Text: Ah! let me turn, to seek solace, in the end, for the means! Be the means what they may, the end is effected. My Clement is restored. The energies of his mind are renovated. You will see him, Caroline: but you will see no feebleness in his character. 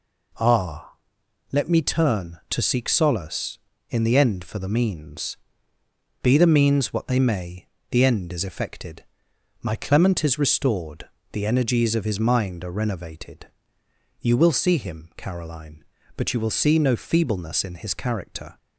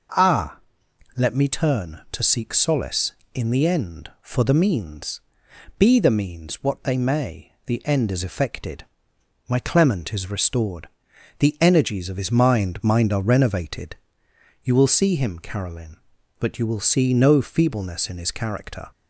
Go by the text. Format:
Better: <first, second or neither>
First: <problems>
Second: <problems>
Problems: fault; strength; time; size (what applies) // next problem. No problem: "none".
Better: first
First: none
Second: says "mind" twice; at 12.8 s